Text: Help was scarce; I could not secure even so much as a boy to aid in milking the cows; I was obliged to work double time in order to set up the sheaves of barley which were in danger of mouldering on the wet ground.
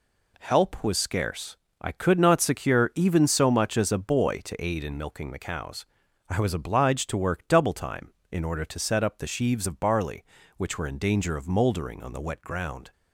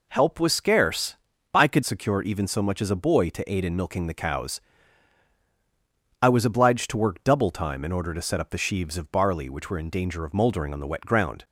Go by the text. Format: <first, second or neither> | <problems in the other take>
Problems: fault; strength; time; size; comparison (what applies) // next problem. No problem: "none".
first | skips "not"; at 1.8 s